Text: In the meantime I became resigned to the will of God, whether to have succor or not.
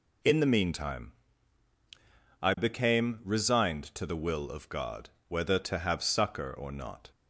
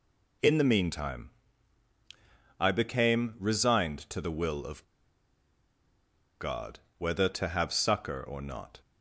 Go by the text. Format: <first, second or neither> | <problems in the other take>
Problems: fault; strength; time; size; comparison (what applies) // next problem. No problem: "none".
first | pauses between "meantime" and "I"; strong; at 1.2 s; 1.3 s long; strong in the first // pauses between "of" and "God"; strong; at 4.8 s; 1.5 s long